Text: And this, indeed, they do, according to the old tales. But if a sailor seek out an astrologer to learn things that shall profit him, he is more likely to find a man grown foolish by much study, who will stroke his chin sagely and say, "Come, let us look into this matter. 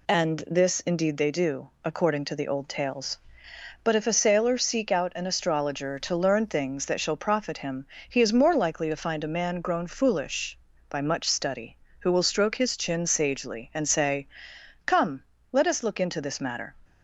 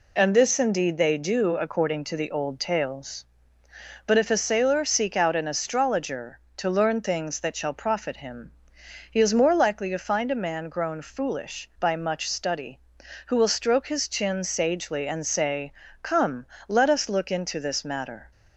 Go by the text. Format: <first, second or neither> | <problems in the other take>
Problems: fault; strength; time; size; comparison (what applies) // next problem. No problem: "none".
neither | none